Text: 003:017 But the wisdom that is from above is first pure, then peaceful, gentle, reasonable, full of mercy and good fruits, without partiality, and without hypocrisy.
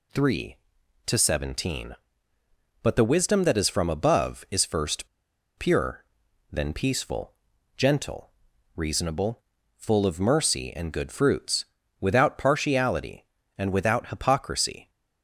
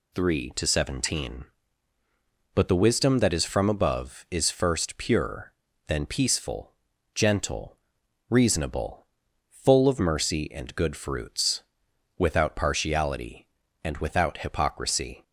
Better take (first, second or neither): second